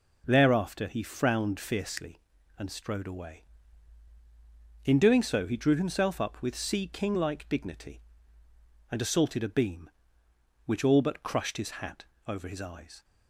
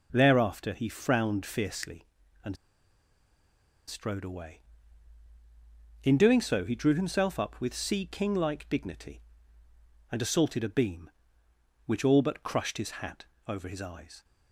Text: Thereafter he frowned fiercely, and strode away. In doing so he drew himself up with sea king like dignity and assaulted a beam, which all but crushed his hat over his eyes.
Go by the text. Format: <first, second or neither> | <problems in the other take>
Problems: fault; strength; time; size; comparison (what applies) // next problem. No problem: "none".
first | pauses between "and" and "strode"; strong; at 2.5 s; 1.3 s long // pauses between "hat" and "over"; slight; at 13.2 s; 0.22 s long; slight in the first